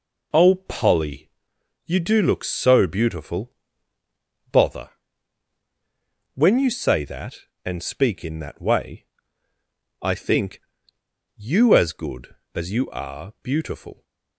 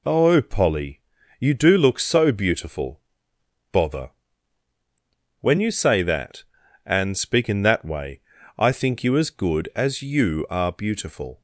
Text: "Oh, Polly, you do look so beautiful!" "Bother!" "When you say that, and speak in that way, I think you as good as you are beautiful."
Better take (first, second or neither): second